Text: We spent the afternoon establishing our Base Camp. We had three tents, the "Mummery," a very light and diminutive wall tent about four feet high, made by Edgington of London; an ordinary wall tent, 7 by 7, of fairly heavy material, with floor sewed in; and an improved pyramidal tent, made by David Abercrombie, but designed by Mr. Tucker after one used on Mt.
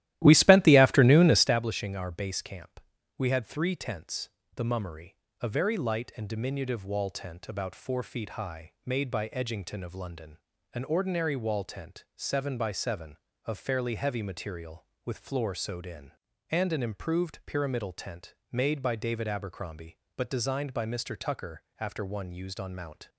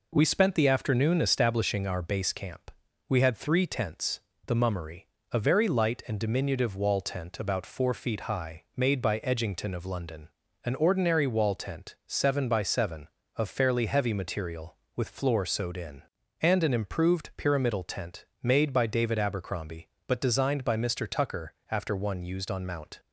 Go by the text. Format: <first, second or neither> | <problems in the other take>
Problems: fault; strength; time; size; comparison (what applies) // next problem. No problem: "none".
second | starts louder than the rest; strong; until 1.7 s; 14 dB // pauses between "Tucker" and "after"; slight; at 21.6 s; 0.18 s long; slight in the second